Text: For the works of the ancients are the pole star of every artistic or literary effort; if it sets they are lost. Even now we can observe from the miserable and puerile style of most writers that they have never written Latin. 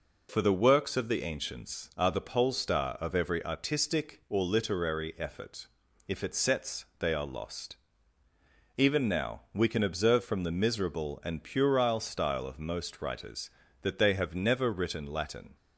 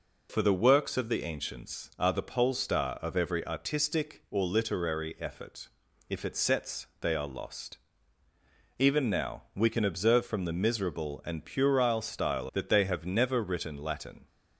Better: first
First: none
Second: skips "of most writers"; at 12.4 s

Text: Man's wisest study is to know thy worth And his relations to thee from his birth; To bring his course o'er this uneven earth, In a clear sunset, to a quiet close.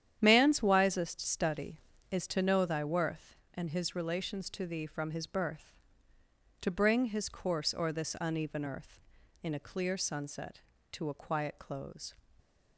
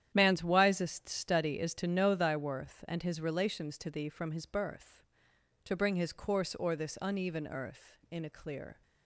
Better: first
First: starts louder than the rest; strong; until 1.2 s; 9.5 dB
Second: starts louder than the rest; strong; until 1.1 s; 10 dB // stops before "sunset to a quiet close"; at 8.8 s

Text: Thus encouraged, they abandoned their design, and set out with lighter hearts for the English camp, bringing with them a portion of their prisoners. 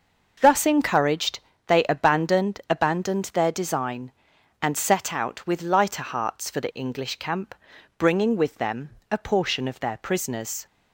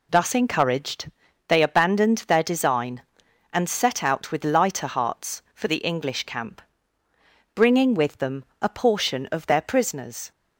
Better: second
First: says "abandoned" twice; at 2.7 s // pauses between "them" and "a"; slight; at 8.8 s; 0.22 s long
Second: none

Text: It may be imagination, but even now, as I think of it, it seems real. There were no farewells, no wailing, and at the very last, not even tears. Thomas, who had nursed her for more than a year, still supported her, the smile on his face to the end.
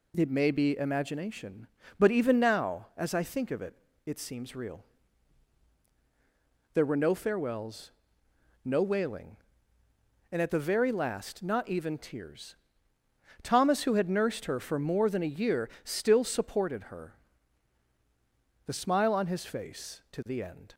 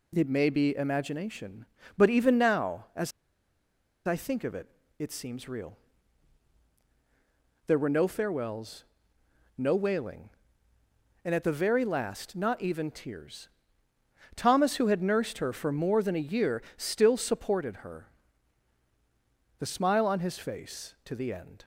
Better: first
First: none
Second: pauses between "as" and "I"; noticeable; at 3.1 s; 0.95 s long

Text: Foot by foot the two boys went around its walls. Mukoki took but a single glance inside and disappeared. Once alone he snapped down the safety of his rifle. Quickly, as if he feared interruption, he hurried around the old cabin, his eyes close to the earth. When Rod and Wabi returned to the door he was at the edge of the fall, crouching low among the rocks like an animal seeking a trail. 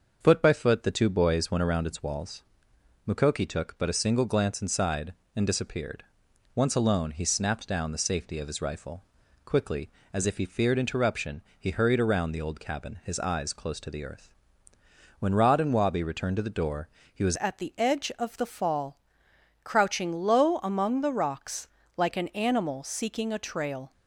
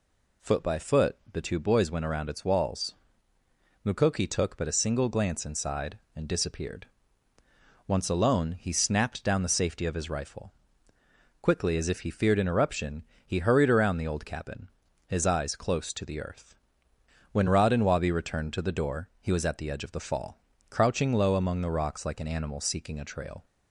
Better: second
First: starts louder than the rest; until 1.2 s; 6.5 dB // pauses between "door" and "he"; slight; at 16.8 s; 0.26 s long // changes voice at "at"; from 17.3 s on; 6.6 s long // pauses between "rocks" and "like"; slight; at 21.6 s; 0.30 s long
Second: none

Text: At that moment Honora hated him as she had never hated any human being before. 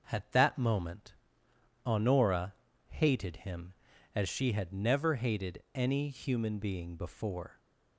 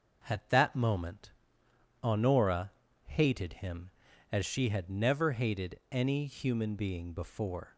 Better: neither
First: starts louder than the rest; noticeable; until 1.1 s; 6 dB // pauses between "moment" and "Honora"; noticeable; at 1.1 s; 0.68 s long // pauses between "Honora" and "hated"; slight; at 2.5 s; 0.35 s long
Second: starts louder than the rest; noticeable; until 1.2 s; 6 dB // pauses between "moment" and "Honora"; noticeable; at 1.3 s; 0.68 s long // pauses between "Honora" and "hated"; slight; at 2.7 s; 0.34 s long

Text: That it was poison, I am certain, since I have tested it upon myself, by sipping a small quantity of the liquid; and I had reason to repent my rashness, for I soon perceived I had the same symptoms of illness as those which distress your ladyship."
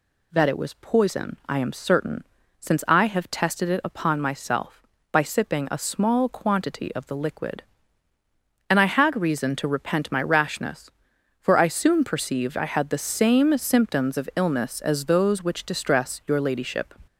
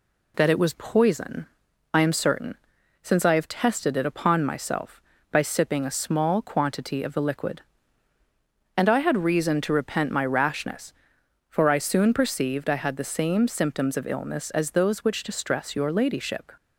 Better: neither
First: none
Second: none

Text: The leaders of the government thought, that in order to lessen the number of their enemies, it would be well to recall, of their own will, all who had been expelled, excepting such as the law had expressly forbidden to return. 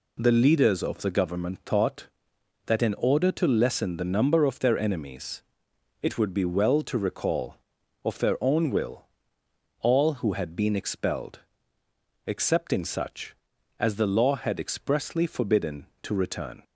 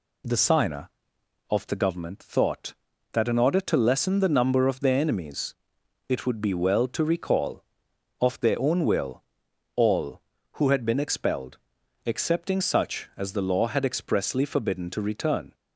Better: first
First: none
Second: says "signer" for "leaders"; at 0.3 s

